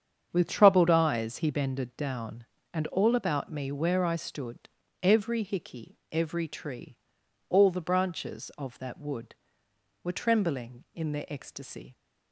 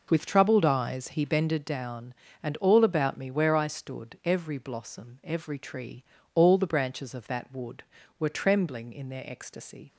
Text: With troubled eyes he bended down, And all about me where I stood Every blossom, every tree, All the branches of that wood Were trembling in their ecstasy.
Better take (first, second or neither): second